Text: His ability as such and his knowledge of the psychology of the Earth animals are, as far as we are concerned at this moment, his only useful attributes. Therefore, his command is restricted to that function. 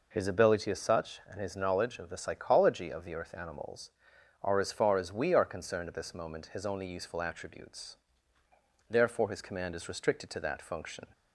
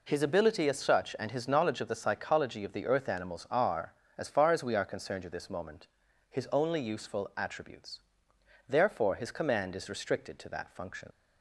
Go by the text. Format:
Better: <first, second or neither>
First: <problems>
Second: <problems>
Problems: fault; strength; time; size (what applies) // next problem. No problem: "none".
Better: first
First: none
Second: leaves "function" unfinished; at 11.1 s; 70 ms